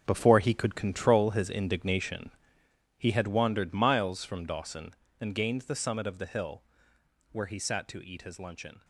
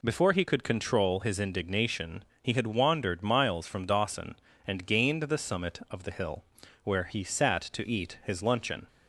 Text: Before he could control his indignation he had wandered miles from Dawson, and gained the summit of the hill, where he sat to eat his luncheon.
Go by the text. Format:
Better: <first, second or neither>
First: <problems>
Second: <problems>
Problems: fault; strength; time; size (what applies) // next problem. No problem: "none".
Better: second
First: gets quieter; strong; throughout; 12.5 dB // pauses between "indignation" and "he"; noticeable; at 2.3 s; 0.66 s long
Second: pauses between "indignation" and "he"; slight; at 2.2 s; 0.16 s long